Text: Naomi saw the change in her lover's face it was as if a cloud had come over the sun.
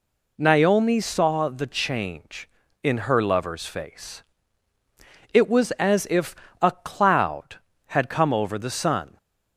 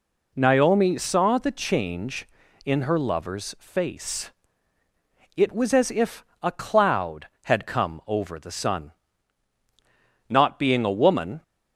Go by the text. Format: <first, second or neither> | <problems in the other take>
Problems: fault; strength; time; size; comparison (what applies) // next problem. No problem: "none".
first | pauses between "face" and "it"; at 4.3 s; 1.0 s long; also in the first // pauses between "if" and "a"; slight; at 6.2 s; 0.18 s long; slight in the first // goes on to say "Not being a woman"; noticeable; from 10.2 s on; 1.1 s long